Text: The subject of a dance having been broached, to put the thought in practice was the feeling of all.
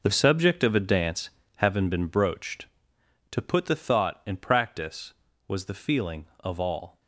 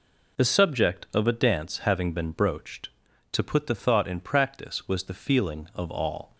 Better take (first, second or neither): second